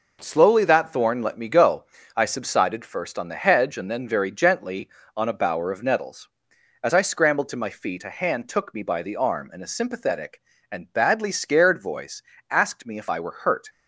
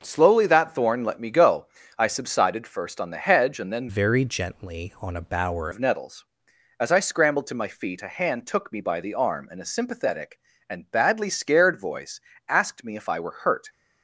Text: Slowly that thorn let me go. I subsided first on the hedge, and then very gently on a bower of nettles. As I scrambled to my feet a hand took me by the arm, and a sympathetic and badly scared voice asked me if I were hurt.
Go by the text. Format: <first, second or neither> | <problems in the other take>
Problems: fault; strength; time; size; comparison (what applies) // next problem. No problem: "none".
first | changes voice from "very" to "bower"; from 3.8 to 5.6 s; 1.8 s long // pauses between "voice" and "asked"; slight; at 12.1 s; 0.30 s long; slight in the first